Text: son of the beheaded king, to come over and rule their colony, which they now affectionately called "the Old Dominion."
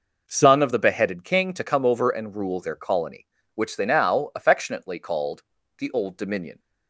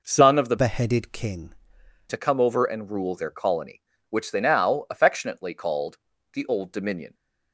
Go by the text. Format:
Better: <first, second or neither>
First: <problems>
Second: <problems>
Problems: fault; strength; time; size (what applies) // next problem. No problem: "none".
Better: first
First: pauses between "called" and "the"; slight; at 5.4 s; 0.36 s long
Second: changes voice from "beheaded" to "king"; from 0.5 to 1.5 s; 1.0 s long // pauses between "called" and "the"; slight; at 5.9 s; 0.36 s long